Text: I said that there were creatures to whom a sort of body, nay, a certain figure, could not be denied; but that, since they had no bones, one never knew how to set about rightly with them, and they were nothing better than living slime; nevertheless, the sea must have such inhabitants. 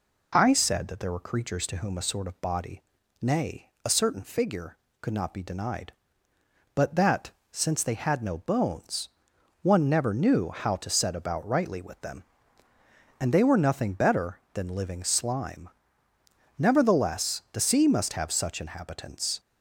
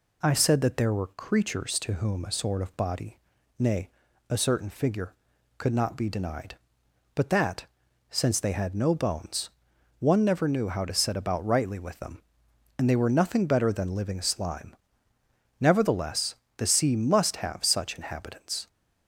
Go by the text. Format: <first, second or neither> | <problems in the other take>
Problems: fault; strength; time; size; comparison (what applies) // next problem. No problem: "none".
neither | none